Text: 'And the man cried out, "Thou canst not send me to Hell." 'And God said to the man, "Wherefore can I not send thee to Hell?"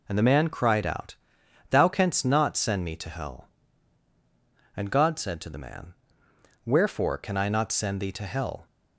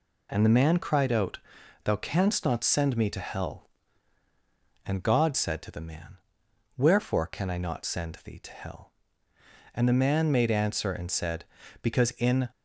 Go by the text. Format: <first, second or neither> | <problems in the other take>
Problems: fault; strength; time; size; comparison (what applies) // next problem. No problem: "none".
first | goes on to say "And the man made answer and said Because in"; strong; from 9.7 s on; 2.7 s long